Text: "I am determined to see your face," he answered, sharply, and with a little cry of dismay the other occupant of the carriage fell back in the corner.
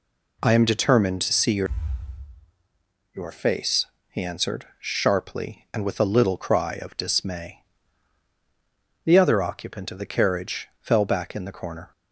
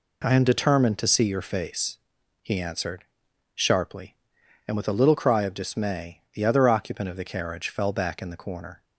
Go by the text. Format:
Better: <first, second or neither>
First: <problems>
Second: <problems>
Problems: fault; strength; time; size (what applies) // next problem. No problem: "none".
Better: second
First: says "your" twice; at 3.1 s // pauses between "dismay" and "the"; strong; at 7.6 s; 1.4 s long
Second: none